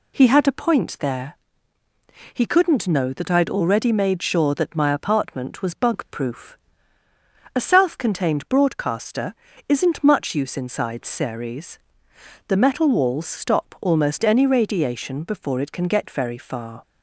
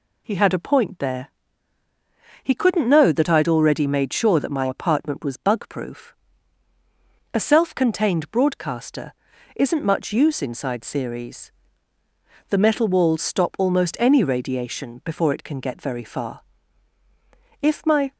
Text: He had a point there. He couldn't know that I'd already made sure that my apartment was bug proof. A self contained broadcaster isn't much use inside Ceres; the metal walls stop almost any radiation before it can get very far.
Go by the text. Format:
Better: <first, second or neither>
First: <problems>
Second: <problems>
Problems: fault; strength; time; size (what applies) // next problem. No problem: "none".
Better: first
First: pauses between "broadcaster" and "isn't"; slight; at 9.3 s; 0.32 s long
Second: pauses between "broadcaster" and "isn't"; at 9.1 s; 0.42 s long // goes on to say "If my"; from 17.6 s on; 0.52 s long